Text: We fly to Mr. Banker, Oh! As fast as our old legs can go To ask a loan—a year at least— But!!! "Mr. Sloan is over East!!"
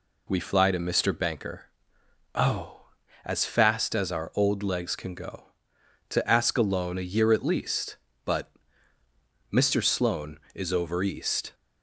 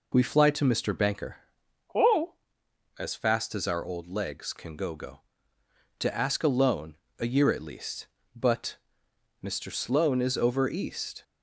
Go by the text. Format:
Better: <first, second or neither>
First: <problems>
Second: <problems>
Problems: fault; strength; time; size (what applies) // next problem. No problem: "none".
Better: first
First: none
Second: says "go" twice; at 4.9 s